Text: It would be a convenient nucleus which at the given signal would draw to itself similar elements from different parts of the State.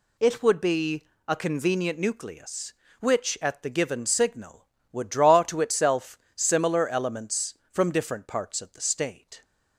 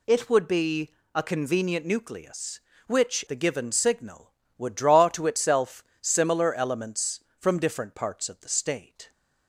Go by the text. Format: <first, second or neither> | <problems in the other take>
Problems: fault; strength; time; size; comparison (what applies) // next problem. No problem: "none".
first | pauses between "be" and "a"; slight; at 0.9 s; 0.24 s long; slight in the first // skips "at"; at 3.2 s // pauses between "itself" and "similar"; slight; at 5.8 s; 0.18 s long; slight in the first